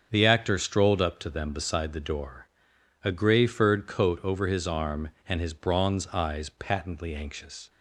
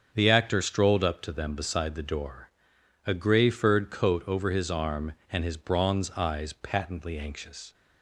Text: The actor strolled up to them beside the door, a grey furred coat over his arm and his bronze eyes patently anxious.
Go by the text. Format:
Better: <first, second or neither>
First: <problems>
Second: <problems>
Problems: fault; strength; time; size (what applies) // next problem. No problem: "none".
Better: neither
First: starts louder than the rest; strong; until 1.1 s; 7.5 dB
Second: starts louder than the rest; strong; until 1.1 s; 7.5 dB